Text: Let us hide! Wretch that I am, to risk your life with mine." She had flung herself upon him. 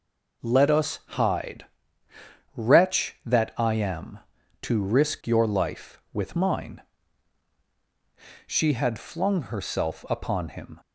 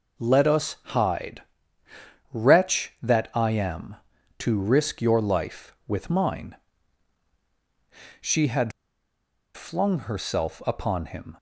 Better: first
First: none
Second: pauses between "had" and "flung"; noticeable; at 8.7 s; 0.85 s long

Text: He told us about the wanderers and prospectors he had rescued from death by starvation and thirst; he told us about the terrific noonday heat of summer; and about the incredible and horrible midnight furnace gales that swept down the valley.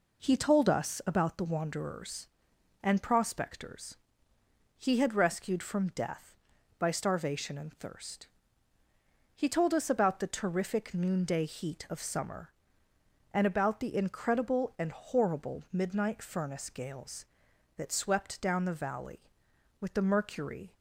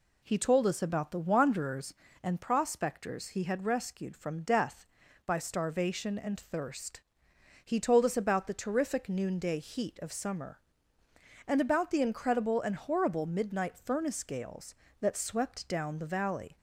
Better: second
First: pauses between "prospectors" and "he"; noticeable; at 3.9 s; 0.81 s long // goes on to say "With the mercury"; noticeable; from 19.7 s on; 0.94 s long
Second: none

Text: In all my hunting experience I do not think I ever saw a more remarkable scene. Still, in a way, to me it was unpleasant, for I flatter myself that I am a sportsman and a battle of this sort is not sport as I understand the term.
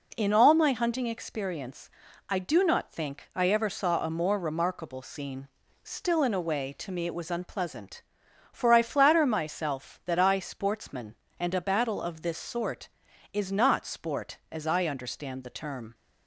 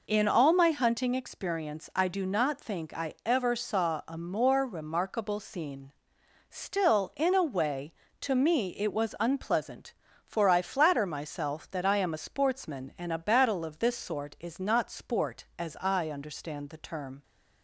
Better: second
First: pauses between "experience" and "I"; at 1.8 s; 0.40 s long // skips "am a"; at 10.3 s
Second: none

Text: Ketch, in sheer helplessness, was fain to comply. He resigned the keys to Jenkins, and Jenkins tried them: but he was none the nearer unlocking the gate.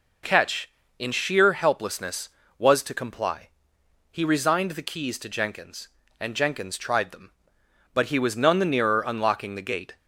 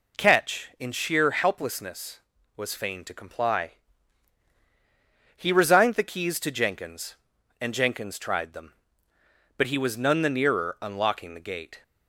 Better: second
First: skips "fain"; at 2.8 s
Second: none

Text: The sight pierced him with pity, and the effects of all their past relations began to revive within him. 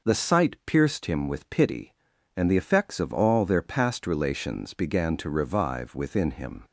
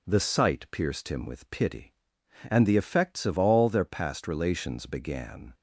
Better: first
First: none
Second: stops before "to revive within him"; at 5.5 s

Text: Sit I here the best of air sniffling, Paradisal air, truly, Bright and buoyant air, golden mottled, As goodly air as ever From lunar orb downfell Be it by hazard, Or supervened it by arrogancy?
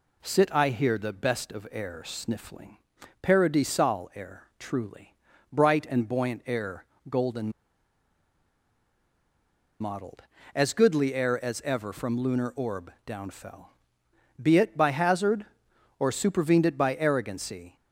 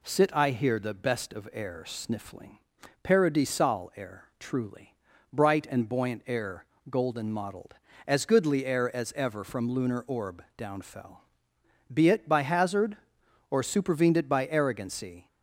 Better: second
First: pauses between "golden" and "mottled"; strong; at 7.5 s; 2.2 s long // pauses between "downfell" and "Be"; noticeable; at 13.6 s; 0.76 s long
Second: pauses between "downfell" and "Be"; noticeable; at 11.1 s; 0.76 s long

